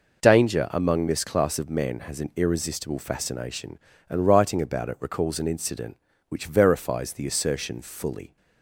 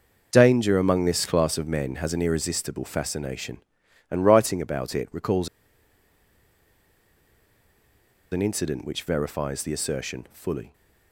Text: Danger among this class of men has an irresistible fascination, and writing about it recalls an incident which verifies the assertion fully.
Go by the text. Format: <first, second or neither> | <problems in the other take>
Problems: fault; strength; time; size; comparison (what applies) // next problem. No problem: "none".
first | pauses between "recalls" and "an"; strong; at 5.4 s; 2.8 s long